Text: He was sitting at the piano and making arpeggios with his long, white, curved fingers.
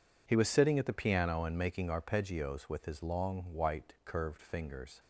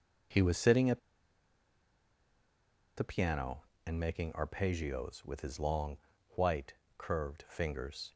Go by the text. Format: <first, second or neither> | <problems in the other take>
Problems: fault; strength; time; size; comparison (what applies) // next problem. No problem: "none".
first | pauses between "at" and "the"; strong; at 0.9 s; 1.9 s long